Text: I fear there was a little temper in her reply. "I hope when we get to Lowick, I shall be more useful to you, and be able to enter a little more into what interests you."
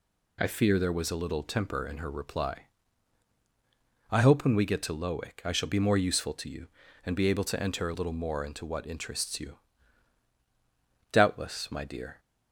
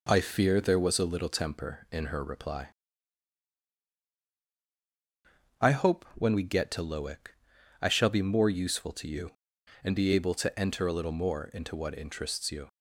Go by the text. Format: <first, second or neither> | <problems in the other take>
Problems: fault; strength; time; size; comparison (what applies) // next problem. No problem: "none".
second | goes on to say "Doubtless my dear"; noticeable; from 11.1 s on; 1.0 s long